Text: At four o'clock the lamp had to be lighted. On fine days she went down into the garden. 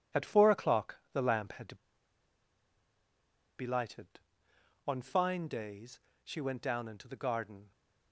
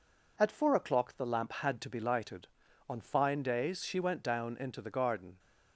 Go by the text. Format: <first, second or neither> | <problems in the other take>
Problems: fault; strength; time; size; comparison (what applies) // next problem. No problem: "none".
second | pauses between "to" and "be"; strong; at 1.7 s; 1.8 s long // pauses between "days" and "she"; slight; at 5.9 s; 0.24 s long